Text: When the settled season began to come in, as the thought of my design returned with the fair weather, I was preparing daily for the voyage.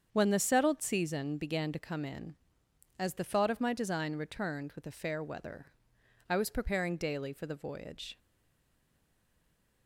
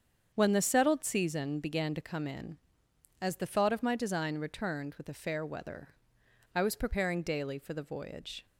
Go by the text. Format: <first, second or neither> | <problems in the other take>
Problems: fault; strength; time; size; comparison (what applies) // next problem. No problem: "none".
second | starts louder than the rest; strong; until 1.1 s; 7.5 dB; strong in the second // stays silent after the last word; noticeable; from 8.1 s on; 1.7 s long